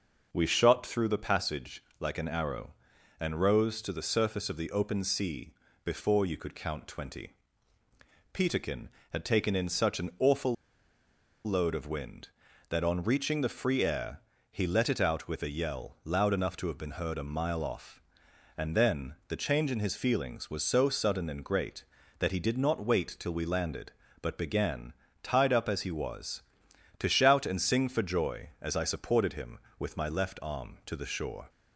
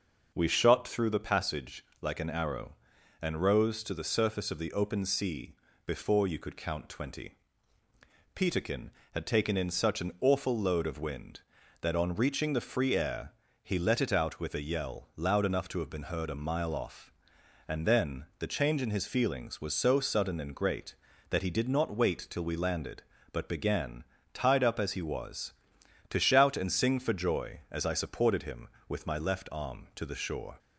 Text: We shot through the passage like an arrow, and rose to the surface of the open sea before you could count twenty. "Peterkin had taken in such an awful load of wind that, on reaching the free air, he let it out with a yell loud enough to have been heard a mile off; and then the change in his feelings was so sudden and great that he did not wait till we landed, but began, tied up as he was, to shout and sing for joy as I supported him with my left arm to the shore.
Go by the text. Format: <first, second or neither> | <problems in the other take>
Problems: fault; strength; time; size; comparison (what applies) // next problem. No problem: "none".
second | starts louder than the rest; until 1.3 s; 6 dB; also in the second // pauses between "passage" and "like"; slight; at 1.8 s; 0.16 s long; slight in the second // pauses between "sea" and "before"; slight; at 5.5 s; 0.30 s long; slight in the second // pauses between "awful" and "load"; noticeable; at 10.5 s; 0.89 s long